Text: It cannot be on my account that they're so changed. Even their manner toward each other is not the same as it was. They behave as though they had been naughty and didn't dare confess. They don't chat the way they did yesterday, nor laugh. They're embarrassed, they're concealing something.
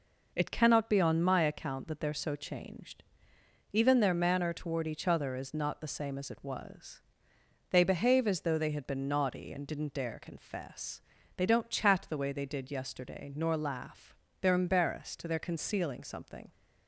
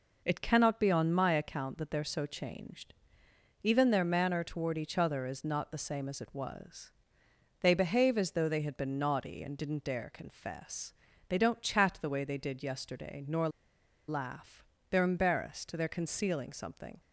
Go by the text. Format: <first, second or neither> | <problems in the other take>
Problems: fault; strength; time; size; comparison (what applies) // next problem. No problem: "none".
first | pauses between "nor" and "laugh"; noticeable; at 13.4 s; 0.59 s long